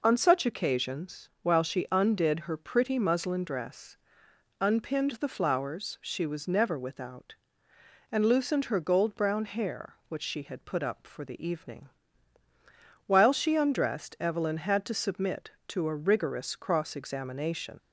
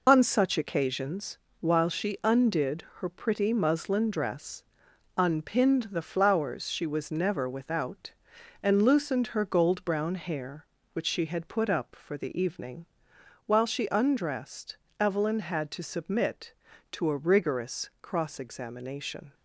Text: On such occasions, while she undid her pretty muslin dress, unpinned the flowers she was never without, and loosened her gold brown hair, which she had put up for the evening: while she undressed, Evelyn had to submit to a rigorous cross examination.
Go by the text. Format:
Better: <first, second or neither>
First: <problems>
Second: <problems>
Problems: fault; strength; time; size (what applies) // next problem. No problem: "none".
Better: first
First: none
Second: loses the start of "On"; at 0.0 s; 55 ms // pauses between "undid" and "her"; slight; at 2.8 s; 0.16 s long